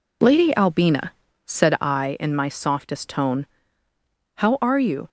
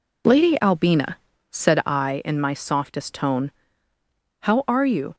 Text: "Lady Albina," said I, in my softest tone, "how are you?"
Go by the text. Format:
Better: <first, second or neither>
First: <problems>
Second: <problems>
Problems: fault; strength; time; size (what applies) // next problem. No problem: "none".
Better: neither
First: none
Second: none